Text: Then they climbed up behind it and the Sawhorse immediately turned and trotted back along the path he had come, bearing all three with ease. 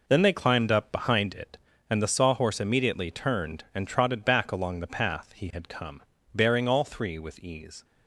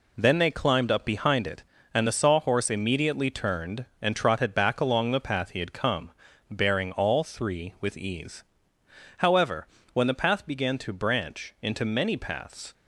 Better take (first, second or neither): first